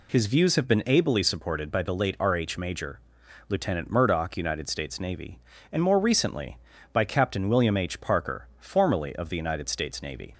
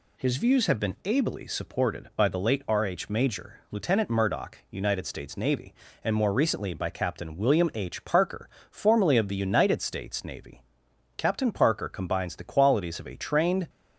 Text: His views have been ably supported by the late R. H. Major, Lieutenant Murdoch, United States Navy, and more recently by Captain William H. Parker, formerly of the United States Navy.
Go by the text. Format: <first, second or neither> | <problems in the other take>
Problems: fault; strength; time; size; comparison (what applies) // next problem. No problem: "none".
first | goes on to say "Captain Parker combines the qualities of a trained"; strong; from 11.1 s on; 2.5 s long